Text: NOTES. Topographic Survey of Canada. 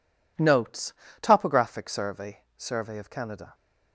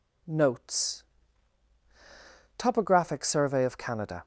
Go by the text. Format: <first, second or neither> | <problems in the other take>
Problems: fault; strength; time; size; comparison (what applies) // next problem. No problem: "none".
second | says "Survey" twice; at 2.5 s